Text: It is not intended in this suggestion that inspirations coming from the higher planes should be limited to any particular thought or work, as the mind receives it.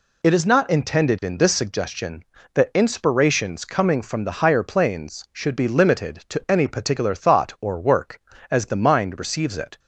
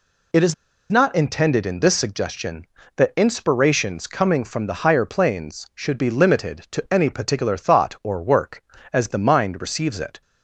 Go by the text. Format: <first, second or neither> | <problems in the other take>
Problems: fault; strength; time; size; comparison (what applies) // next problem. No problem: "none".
first | pauses between "is" and "not"; at 0.5 s; 0.38 s long